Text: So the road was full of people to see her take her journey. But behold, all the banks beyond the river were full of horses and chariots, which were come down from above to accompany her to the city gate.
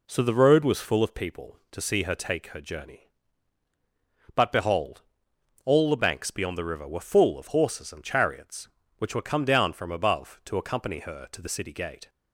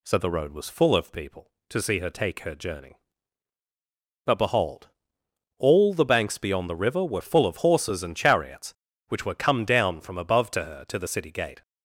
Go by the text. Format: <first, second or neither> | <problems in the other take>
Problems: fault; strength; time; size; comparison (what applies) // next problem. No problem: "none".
first | skips "accompany"; at 10.6 s